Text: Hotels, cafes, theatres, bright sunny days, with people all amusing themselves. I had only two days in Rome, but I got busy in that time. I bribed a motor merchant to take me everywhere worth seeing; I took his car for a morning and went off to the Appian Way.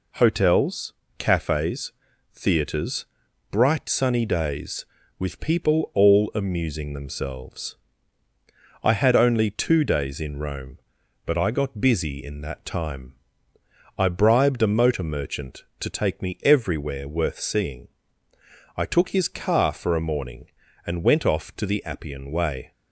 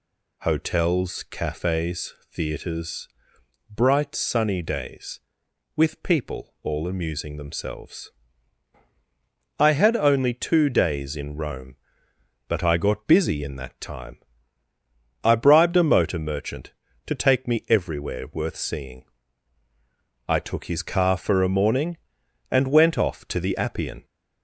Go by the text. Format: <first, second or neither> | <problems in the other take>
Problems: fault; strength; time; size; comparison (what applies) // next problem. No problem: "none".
first | stops before "Way"; at 24.0 s